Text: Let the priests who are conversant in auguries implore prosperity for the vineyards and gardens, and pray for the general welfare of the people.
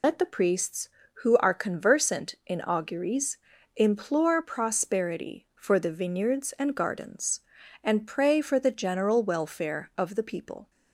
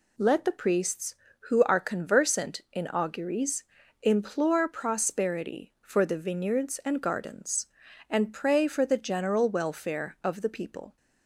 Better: second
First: loses the start of "Let"; at 0.0 s; 120 ms // pauses between "auguries" and "implore"; at 3.3 s; 0.38 s long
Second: pauses between "auguries" and "implore"; at 3.6 s; 0.38 s long

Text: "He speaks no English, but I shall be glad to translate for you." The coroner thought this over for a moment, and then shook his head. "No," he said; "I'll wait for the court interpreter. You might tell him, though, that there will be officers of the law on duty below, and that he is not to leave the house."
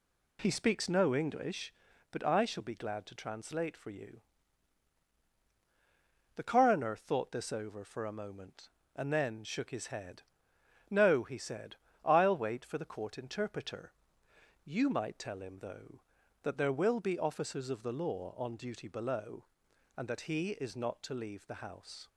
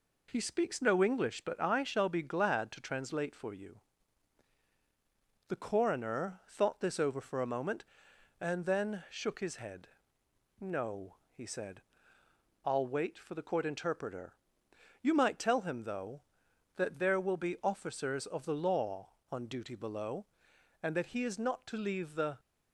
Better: first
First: none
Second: stops before "house"; at 22.3 s

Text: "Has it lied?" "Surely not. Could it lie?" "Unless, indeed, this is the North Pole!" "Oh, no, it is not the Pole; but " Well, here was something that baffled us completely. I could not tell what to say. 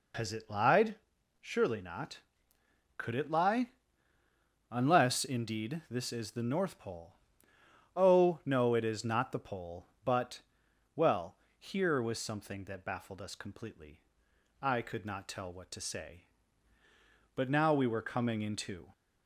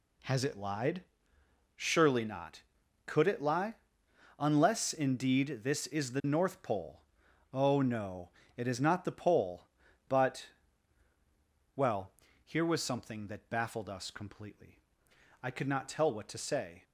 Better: second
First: goes on to say "But now we were coming into"; from 17.3 s on; 1.5 s long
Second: none

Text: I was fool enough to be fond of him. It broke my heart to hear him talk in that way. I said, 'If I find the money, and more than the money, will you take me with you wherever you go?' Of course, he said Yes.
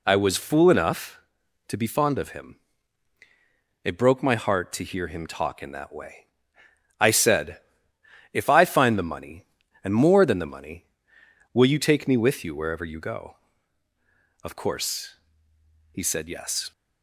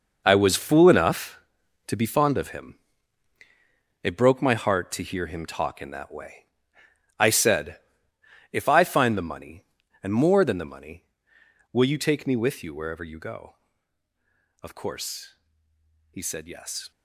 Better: first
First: none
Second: gets quieter; strong; throughout; 11.5 dB

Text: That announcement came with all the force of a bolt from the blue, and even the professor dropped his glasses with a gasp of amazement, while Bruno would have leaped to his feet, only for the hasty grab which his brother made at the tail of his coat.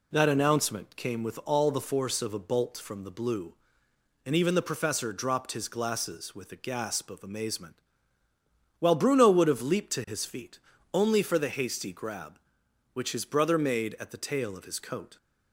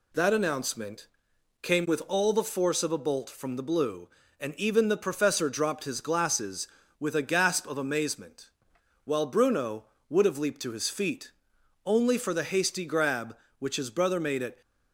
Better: first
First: none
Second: pauses between "announcement" and "came"; noticeable; at 1.0 s; 0.54 s long // stops before "the tail of his coat"; at 14.6 s

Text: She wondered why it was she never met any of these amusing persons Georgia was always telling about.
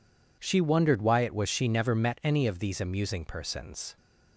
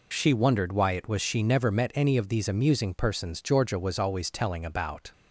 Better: second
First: stops before "Georgia was always telling about"; at 3.9 s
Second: none

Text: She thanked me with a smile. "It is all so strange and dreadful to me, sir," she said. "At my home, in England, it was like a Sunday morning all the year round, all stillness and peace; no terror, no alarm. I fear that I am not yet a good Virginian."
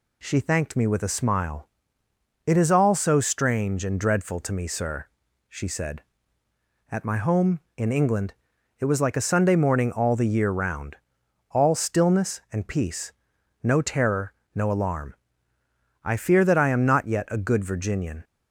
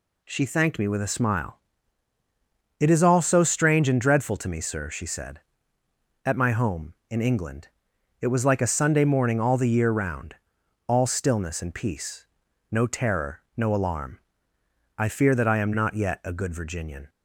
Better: neither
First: none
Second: none

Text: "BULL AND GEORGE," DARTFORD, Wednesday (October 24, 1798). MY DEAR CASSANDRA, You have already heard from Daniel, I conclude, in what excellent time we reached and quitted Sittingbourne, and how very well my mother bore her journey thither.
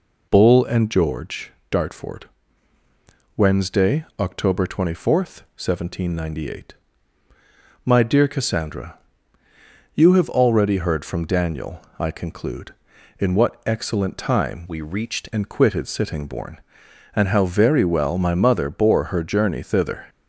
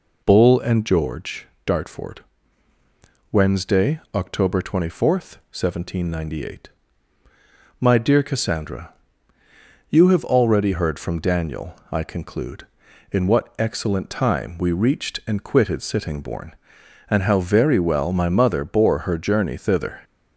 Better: second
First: changes voice from "we" to "reached"; from 14.6 to 15.2 s; 0.6 s long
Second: none

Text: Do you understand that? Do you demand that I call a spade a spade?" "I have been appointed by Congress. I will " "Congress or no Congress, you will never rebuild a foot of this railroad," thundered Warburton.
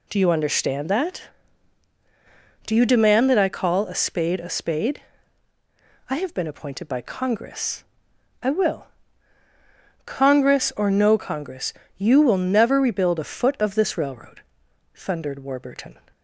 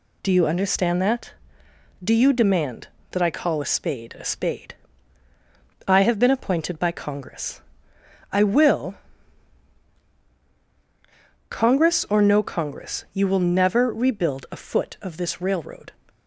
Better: first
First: none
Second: stops before "thundered Warburton"; at 16.0 s

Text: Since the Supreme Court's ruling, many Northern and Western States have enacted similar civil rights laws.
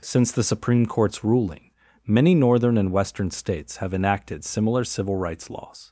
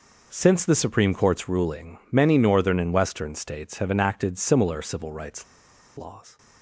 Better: first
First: none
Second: pauses between "rights" and "laws"; noticeable; at 5.4 s; 0.53 s long

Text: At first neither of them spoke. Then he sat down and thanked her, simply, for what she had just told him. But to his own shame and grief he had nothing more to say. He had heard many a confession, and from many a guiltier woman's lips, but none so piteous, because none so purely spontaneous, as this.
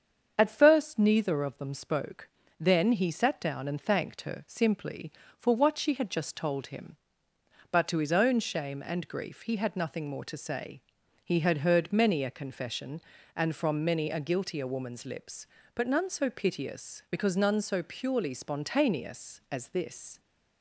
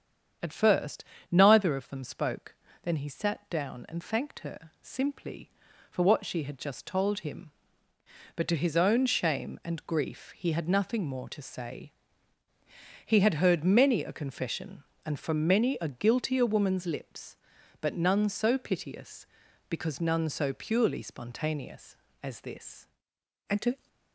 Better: first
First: starts louder than the rest; strong; until 1.3 s; 7.5 dB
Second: starts louder than the rest; strong; until 1.7 s; 8 dB // pauses between "first" and "neither"; slight; at 1.0 s; 0.28 s long // goes on to say "And to"; slight; from 23.4 s on; 0.38 s long

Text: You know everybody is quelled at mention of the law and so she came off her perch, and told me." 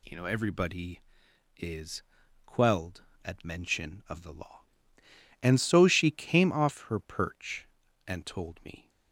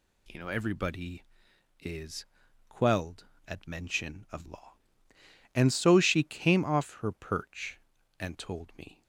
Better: first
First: pauses between "is" and "quelled"; at 2.0 s; 0.44 s long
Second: pauses between "is" and "quelled"; at 2.2 s; 0.44 s long // skips "the"; at 4.4 s

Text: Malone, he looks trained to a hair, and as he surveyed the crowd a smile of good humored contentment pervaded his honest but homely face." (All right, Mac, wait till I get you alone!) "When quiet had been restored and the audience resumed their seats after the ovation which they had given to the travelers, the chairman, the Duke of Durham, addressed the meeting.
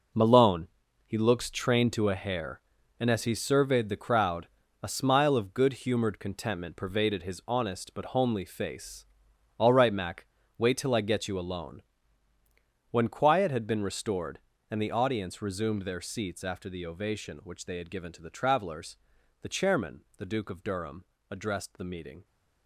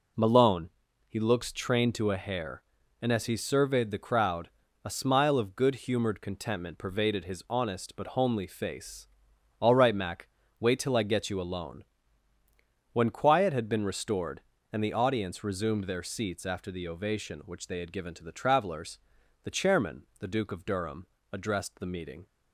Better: second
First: gets quieter; strong; throughout; 11.5 dB // pauses between "crowd" and "a"; slight; at 4.4 s; 0.36 s long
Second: pauses between "crowd" and "a"; slight; at 4.4 s; 0.36 s long

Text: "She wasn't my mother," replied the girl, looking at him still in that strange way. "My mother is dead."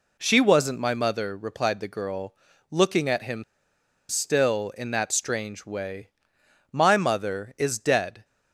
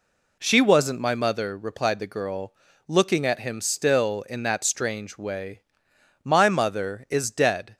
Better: second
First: pauses between "him" and "still"; noticeable; at 3.4 s; 0.65 s long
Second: none

